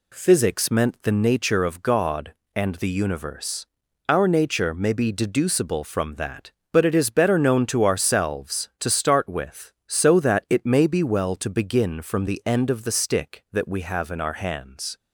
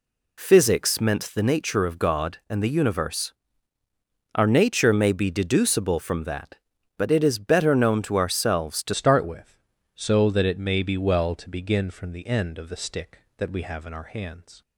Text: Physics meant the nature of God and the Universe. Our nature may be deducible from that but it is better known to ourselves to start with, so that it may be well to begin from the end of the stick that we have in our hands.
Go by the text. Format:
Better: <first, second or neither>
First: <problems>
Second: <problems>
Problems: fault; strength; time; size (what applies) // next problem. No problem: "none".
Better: first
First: none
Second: changes voice at "start"; from 8.9 s on; 5.7 s long